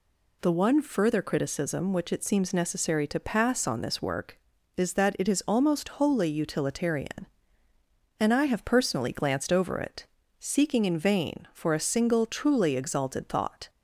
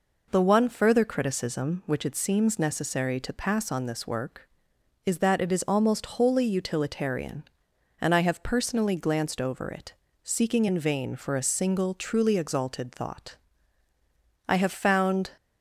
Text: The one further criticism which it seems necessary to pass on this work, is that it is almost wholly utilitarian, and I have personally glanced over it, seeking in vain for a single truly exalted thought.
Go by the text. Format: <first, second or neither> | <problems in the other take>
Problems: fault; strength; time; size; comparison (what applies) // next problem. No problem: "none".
first | goes on to say "I have found"; noticeable; from 14.4 s on; 0.82 s long